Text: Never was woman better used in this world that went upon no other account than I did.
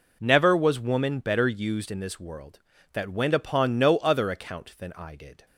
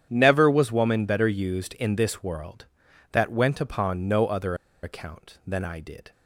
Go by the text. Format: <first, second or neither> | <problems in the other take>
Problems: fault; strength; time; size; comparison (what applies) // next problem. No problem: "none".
first | starts louder than the rest; strong; until 1.1 s; 9.5 dB // pauses between "other" and "account"; slight; at 4.5 s; 0.28 s long